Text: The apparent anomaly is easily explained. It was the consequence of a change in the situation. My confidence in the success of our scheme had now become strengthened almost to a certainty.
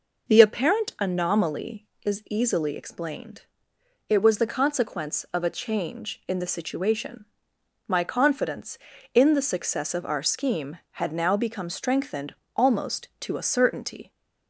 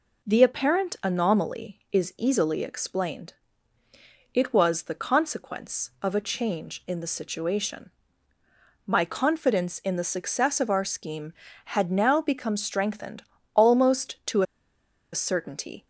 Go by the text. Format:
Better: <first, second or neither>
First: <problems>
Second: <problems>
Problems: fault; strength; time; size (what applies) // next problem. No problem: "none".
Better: first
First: pauses between "strengthened" and "almost"; slight; at 12.3 s; 0.22 s long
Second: pauses between "strengthened" and "almost"; slight; at 13.2 s; 0.32 s long // pauses between "to" and "a"; noticeable; at 14.4 s; 0.70 s long